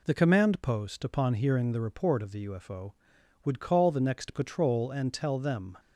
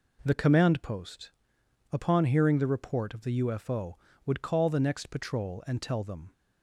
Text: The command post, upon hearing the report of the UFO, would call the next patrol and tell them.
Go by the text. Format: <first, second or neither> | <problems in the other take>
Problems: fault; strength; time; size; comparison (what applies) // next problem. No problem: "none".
neither | none